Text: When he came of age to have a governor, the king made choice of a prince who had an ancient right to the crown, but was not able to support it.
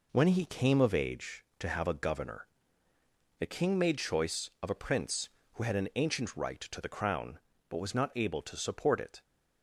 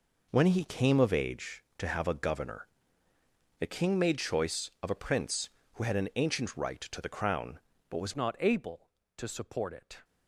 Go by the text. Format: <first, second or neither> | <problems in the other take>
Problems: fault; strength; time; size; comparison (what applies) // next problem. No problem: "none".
first | changes voice at "not"; from 8.1 s on; 1.9 s long